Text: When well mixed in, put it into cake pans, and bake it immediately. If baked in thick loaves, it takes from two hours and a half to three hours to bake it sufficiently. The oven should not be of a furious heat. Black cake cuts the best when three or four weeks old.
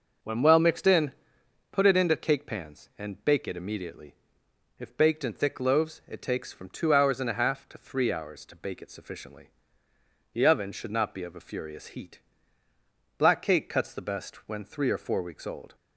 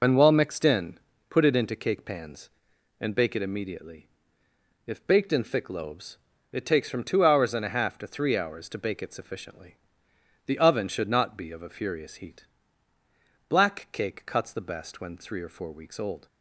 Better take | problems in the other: first | loses the start of "When"; at 0.0 s; 55 ms

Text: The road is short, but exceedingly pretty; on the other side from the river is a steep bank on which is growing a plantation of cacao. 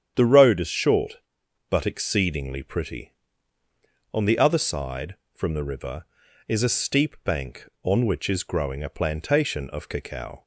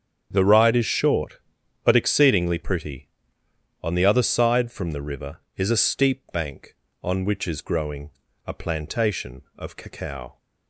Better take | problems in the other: first | starts louder than the rest; strong; until 1.3 s; 7.5 dB; strong in the first // says "ride" for "road"; at 0.4 s // pauses between "growing" and "a"; slight; at 8.1 s; 0.34 s long

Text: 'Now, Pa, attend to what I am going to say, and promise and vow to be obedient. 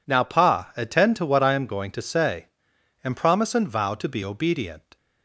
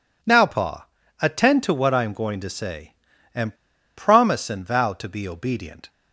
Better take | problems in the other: first | pauses between "and" and "promise"; at 3.5 s; 0.42 s long

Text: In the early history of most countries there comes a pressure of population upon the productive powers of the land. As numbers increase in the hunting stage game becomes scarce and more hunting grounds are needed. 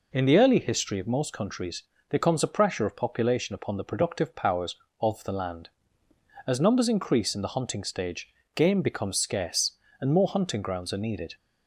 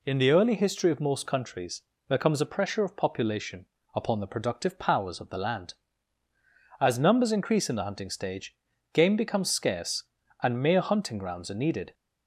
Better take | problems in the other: first | pauses between "countries" and "there"; slight; at 1.8 s; 0.24 s long; slight in the first // pauses between "population" and "upon"; slight; at 3.6 s; 0.30 s long // pauses between "stage" and "game"; slight; at 8.5 s; 0.36 s long; slight in the first // says "mere" for "more"; at 10.6 s

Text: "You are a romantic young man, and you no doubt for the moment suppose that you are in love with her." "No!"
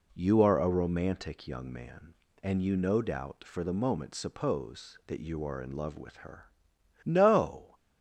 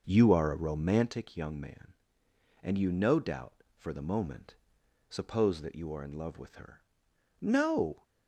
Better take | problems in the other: first | starts louder than the rest; noticeable; until 1.1 s; 5.5 dB // pauses between "moment" and "suppose"; noticeable; at 4.5 s; 0.56 s long

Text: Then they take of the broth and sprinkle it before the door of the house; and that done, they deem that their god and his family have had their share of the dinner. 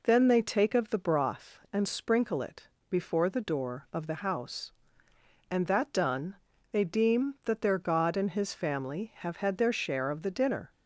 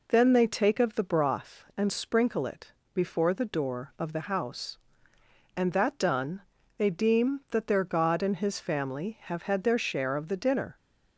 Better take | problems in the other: neither | pauses between "it" and "before"; slight; the same in both

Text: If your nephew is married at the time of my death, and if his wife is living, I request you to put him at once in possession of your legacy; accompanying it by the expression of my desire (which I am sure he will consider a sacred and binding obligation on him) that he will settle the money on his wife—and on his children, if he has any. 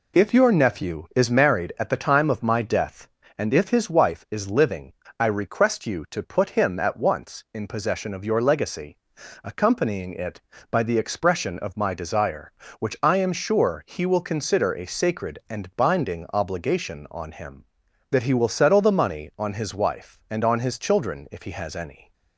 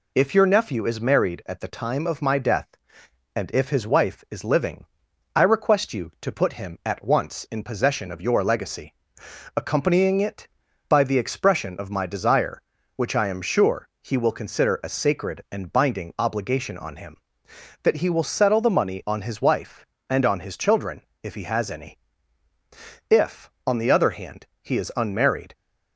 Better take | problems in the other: first | goes on to say "If on the other hand he is unmarried"; strong; from 23.1 s on; 2.4 s long

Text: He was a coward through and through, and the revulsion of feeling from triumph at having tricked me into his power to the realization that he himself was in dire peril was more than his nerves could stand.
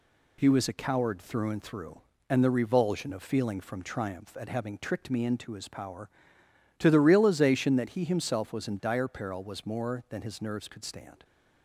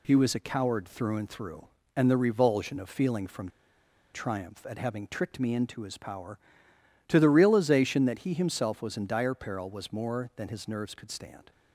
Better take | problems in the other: first | pauses between "from" and "triumph"; noticeable; at 3.4 s; 0.65 s long

